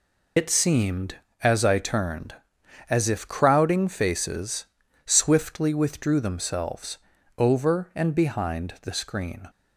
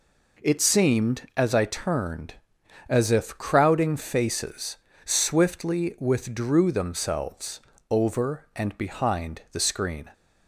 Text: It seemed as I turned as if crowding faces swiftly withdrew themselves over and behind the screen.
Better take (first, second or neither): second